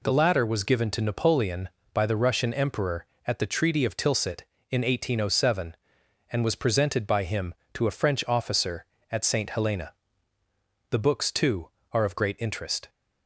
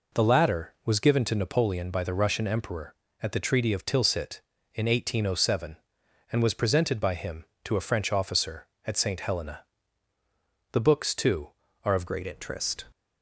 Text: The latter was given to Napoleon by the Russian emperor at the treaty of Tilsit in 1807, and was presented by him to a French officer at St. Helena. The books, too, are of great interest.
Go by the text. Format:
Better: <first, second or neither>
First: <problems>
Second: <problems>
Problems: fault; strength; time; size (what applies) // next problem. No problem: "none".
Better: first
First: none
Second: changes voice at "great"; from 12.0 s on; 0.8 s long